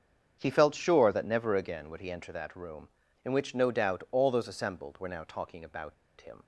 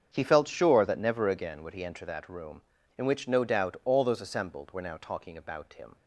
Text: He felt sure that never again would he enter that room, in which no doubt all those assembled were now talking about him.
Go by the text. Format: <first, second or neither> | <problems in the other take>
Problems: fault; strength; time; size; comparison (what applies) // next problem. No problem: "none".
second | starts louder than the rest; strong; until 1.4 s; 7.5 dB; strong in the second // pauses between "about" and "him"; slight; at 5.9 s; 0.26 s long